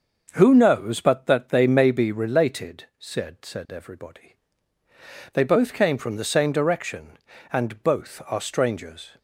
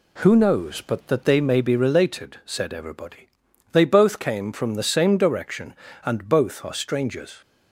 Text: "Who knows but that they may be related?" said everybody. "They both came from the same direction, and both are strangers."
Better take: second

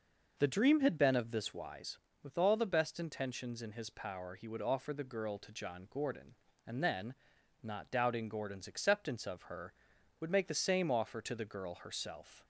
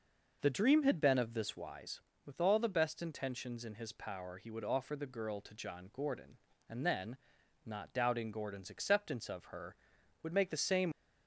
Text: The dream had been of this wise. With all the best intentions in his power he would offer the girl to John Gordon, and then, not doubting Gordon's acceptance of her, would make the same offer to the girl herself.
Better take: first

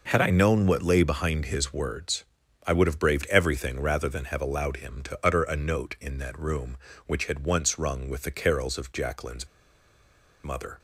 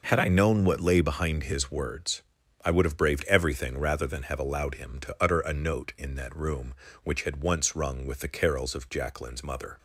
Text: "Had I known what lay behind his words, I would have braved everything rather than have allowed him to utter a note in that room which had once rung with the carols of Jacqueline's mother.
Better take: second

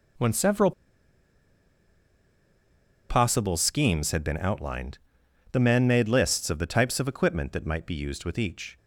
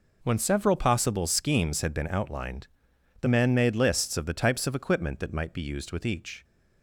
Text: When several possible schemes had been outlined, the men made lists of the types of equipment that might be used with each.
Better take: second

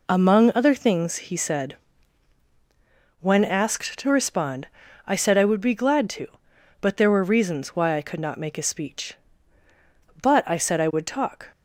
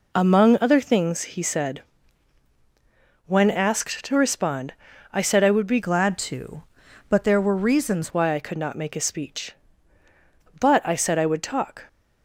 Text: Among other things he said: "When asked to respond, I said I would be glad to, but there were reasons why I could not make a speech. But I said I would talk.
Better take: first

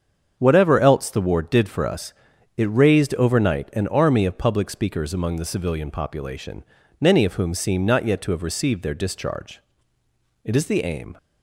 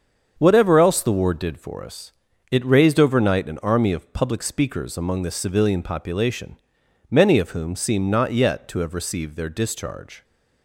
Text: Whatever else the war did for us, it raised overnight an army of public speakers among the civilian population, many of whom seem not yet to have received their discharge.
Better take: second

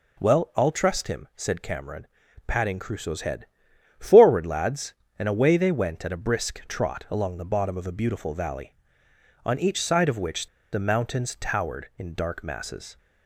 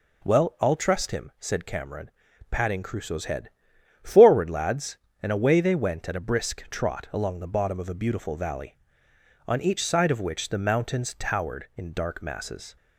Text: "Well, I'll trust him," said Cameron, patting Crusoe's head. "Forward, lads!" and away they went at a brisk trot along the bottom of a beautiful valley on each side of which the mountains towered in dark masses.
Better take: second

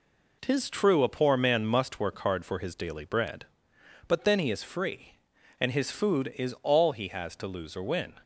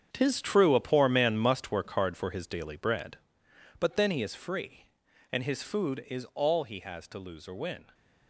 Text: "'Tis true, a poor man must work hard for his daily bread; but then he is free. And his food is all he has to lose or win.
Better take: first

